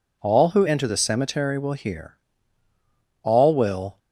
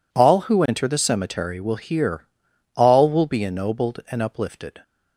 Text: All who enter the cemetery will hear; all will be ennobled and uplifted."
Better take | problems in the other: second | stops before "be ennobled and uplifted"; at 3.9 s

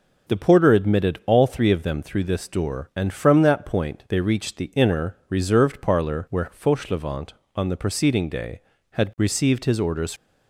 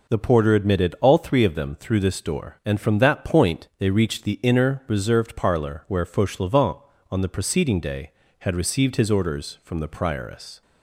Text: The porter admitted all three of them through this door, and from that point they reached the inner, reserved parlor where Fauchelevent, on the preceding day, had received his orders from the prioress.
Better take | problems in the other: second | stops before "from the prioress"; at 10.1 s

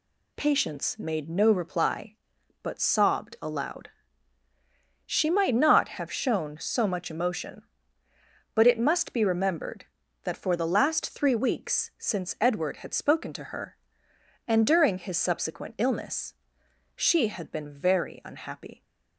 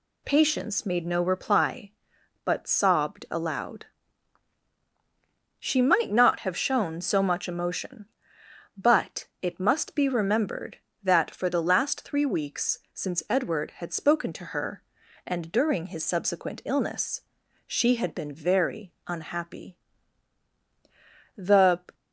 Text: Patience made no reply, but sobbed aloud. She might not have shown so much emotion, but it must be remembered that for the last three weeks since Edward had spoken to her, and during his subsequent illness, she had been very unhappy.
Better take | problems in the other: first | pauses between "but" and "it"; slight; at 9.2 s; 0.16 s long // goes on to say "The"; from 21.3 s on; 0.58 s long

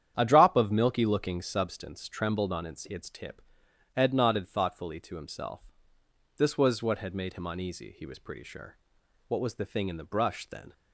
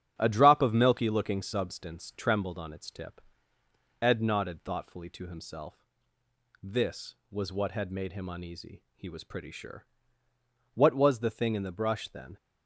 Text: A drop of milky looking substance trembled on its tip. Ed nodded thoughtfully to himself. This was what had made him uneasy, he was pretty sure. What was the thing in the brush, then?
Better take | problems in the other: second | starts louder than the rest; strong; until 1.1 s; 9.5 dB; strong in the second // says "its" twice; at 2.8 s

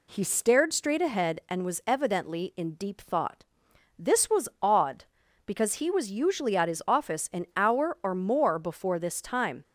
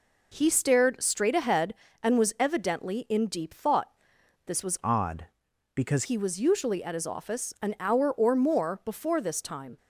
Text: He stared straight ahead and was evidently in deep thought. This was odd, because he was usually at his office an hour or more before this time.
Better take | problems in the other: first | changes voice from "odd" to "because"; from 4.8 to 6.0 s; 1.2 s long

